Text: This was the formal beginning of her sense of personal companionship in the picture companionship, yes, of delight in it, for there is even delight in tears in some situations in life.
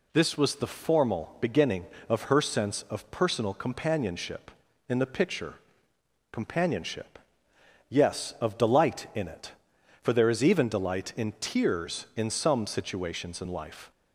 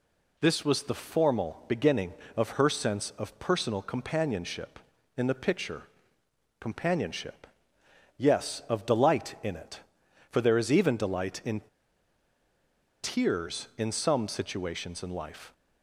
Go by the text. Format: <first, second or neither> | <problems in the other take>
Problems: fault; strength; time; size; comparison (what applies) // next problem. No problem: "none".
first | pauses between "picture" and "companionship"; noticeable; at 5.8 s; 0.76 s long; noticeable in the first // pauses between "in" and "tears"; strong; at 11.6 s; 1.4 s long